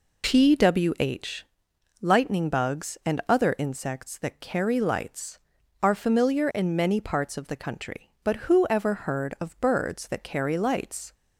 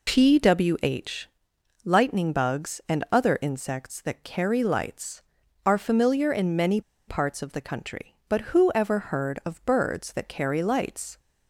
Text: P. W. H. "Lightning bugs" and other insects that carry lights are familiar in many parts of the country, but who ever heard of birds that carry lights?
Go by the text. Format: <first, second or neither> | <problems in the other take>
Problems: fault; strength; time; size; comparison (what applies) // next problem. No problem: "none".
first | pauses between "H" and "Lightning"; noticeable; at 1.2 s; 0.56 s long; noticeable in the first // pauses between "many" and "parts"; slight; at 6.8 s; 0.27 s long